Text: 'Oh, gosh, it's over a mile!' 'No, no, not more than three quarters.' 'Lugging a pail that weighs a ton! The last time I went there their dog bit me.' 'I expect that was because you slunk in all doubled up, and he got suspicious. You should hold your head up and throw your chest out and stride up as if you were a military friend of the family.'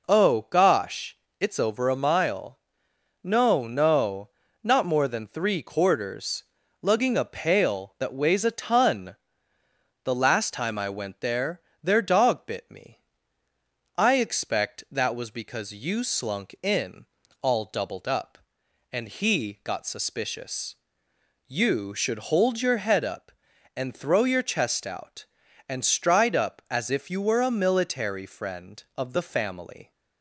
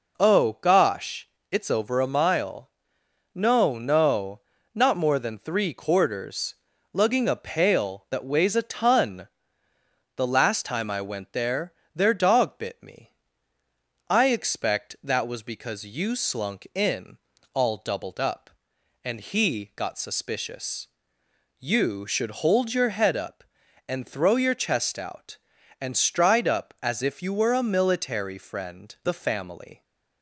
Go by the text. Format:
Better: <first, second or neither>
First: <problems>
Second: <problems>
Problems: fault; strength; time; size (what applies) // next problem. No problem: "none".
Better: first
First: pauses between "there" and "their"; slight; at 11.6 s; 0.20 s long // pauses between "in" and "all"; slight; at 17.0 s; 0.36 s long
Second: pauses between "there" and "their"; slight; at 11.7 s; 0.20 s long // pauses between "in" and "all"; slight; at 17.1 s; 0.36 s long // skips "of"; at 28.9 s